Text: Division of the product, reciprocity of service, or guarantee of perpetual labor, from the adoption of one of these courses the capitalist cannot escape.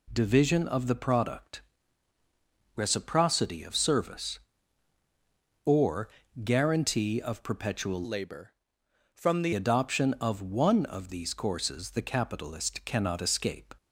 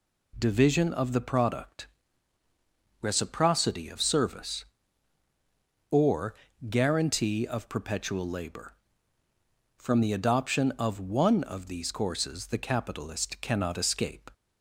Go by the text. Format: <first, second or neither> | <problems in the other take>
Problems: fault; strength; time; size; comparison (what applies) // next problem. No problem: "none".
second | pauses between "or" and "guarantee"; slight; at 6.0 s; 0.34 s long; slight in the second // changes voice from "labor" to "the"; from 8.0 to 9.5 s; 1.5 s long